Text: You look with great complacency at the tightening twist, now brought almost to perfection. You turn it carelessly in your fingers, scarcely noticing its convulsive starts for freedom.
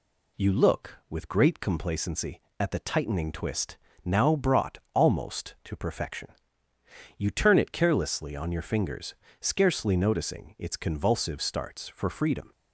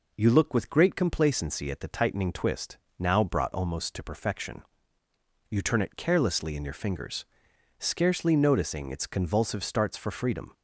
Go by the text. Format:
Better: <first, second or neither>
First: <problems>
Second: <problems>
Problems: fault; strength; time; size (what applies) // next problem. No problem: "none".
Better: second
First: says "on" for "in"; at 8.3 s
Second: none